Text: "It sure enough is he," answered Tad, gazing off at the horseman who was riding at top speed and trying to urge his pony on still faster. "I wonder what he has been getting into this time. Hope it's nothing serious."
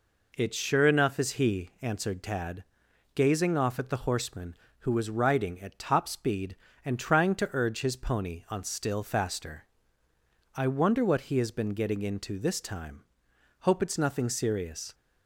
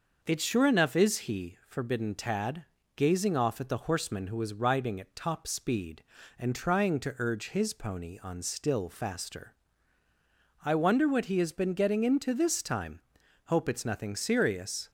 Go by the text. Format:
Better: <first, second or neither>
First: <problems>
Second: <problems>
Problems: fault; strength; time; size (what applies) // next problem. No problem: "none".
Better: first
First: none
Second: starts louder than the rest; noticeable; until 1.2 s; 6 dB // says "forbidden" for "answered"; at 1.6 s